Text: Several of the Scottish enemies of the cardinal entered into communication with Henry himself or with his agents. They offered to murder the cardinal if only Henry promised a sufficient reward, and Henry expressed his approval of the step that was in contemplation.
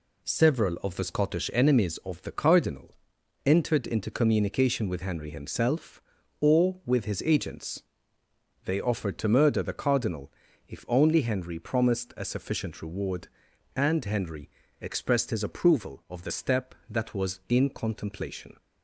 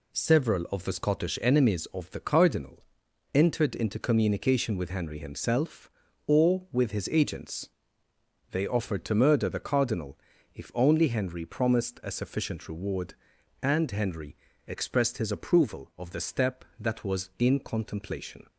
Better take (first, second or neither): neither